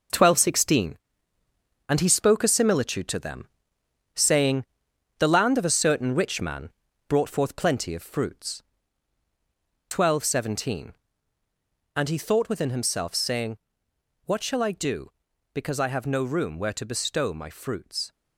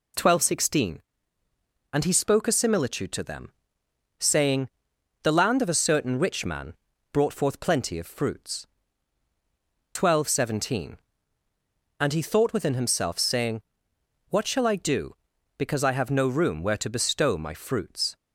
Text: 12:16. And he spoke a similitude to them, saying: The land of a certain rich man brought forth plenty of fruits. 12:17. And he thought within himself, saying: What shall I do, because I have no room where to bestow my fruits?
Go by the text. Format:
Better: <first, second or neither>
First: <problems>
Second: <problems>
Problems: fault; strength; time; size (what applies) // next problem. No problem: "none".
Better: second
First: gets quieter; strong; throughout; 7.5 dB // pauses between "man" and "brought"; at 6.6 s; 0.38 s long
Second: pauses between "man" and "brought"; at 6.7 s; 0.38 s long